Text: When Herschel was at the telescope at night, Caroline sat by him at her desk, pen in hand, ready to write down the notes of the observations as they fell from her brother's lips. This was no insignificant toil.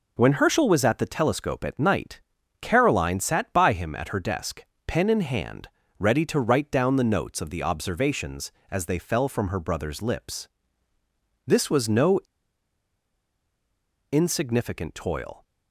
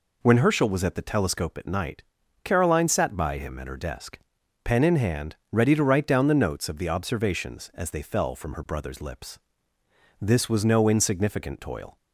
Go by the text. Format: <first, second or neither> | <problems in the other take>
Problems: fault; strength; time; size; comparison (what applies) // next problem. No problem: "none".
second | pauses between "no" and "insignificant"; strong; at 12.1 s; 1.9 s long